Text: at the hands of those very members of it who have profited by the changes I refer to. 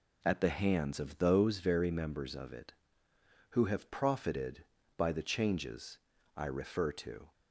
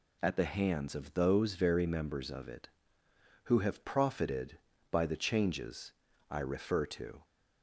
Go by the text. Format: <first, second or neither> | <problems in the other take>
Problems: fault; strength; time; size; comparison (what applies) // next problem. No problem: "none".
second | starts louder than the rest; slight; until 1.7 s; 2 dB // pauses between "changes" and "I"; at 5.9 s; 0.38 s long; also in the second